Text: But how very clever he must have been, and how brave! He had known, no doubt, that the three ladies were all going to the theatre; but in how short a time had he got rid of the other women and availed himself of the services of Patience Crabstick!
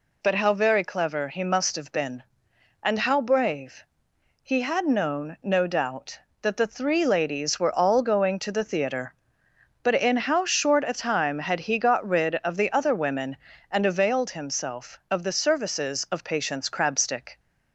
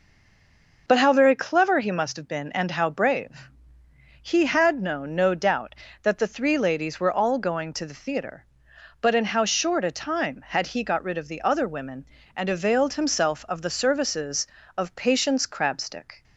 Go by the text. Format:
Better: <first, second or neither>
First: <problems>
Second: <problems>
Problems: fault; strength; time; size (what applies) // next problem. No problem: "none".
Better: first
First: none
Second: stays silent before the first word; slight; until 0.8 s; 0.8 s long